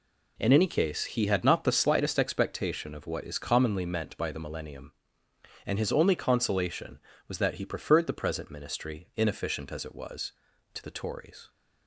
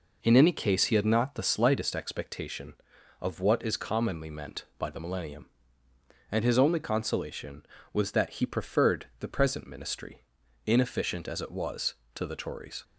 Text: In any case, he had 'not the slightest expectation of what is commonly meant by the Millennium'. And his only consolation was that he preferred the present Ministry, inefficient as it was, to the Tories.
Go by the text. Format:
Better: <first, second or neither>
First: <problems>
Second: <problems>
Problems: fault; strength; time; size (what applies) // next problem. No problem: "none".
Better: neither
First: none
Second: none